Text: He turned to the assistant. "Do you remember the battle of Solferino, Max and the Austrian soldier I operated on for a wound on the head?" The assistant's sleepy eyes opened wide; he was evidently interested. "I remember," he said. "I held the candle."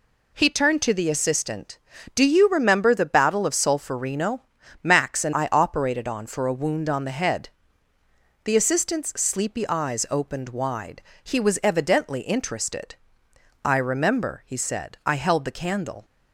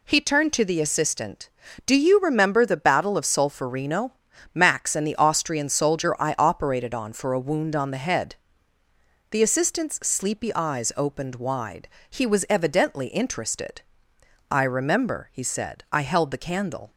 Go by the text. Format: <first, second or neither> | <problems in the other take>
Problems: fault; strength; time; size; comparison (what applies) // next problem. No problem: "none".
second | skips "the Austrian soldier"; at 5.3 s